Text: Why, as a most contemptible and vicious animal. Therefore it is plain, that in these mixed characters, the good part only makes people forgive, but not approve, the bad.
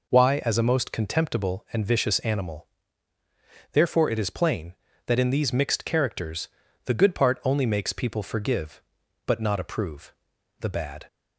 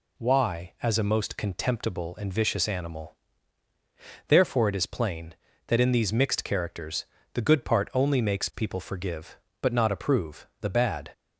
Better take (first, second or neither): neither